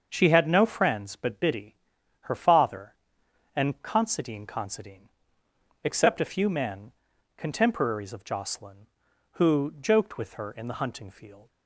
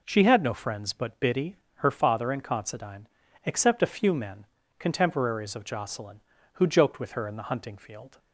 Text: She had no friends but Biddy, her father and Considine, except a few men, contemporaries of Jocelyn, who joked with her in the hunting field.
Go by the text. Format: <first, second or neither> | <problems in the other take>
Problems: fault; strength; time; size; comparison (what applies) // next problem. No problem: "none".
second | starts louder than the rest; until 1.1 s; 6.5 dB // says "Considine" twice; at 4.4 s